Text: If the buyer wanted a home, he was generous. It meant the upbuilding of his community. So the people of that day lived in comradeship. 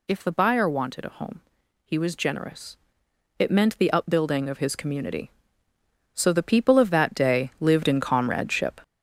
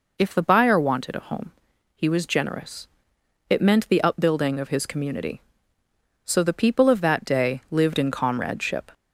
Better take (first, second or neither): second